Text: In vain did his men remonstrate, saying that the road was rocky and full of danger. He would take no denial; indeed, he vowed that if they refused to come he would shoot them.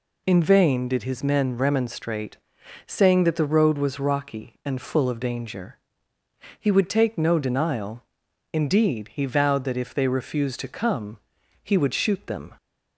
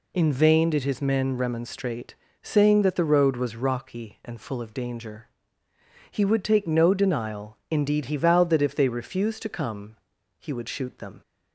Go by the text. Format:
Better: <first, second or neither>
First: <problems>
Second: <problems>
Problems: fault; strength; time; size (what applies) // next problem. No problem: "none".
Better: neither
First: pauses between "come" and "he"; noticeable; at 11.1 s; 0.46 s long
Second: pauses between "come" and "he"; at 9.9 s; 0.42 s long